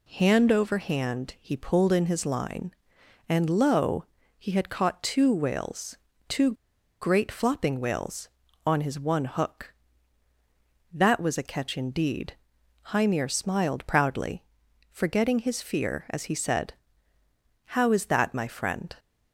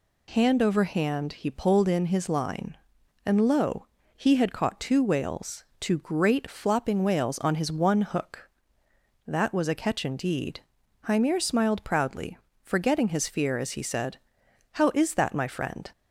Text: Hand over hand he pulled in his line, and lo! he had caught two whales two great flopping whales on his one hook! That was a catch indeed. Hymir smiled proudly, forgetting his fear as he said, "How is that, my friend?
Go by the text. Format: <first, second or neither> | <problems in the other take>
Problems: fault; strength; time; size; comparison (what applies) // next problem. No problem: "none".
second | pauses between "whales" and "two"; slight; at 5.9 s; 0.32 s long; slight in the second // pauses between "two" and "great"; noticeable; at 6.4 s; 0.52 s long